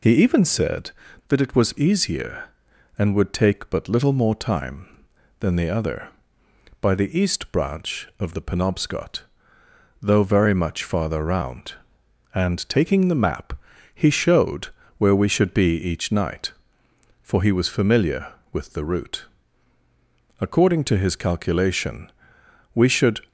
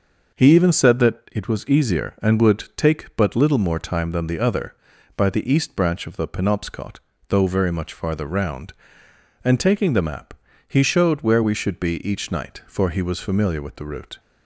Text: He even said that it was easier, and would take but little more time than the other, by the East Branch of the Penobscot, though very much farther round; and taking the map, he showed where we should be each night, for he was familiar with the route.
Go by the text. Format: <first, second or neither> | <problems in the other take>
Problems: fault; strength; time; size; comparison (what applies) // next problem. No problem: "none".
second | pauses between "showed" and "where"; slight; at 14.6 s; 0.28 s long // goes on to say "According to his calculation we should"; strong; from 20.3 s on; 2.8 s long